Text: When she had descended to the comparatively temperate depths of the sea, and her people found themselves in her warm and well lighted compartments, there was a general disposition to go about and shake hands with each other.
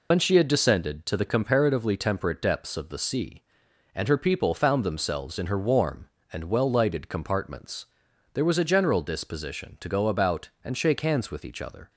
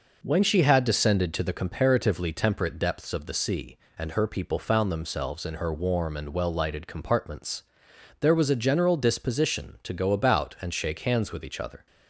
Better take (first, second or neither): second